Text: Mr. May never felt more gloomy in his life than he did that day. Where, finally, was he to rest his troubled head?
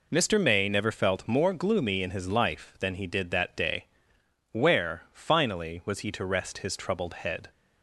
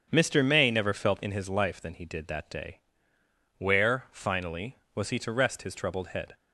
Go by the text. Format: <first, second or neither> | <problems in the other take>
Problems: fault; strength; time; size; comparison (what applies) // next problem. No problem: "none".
first | starts louder than the rest; until 1.1 s; 7 dB // skips "more gloomy"; at 1.2 s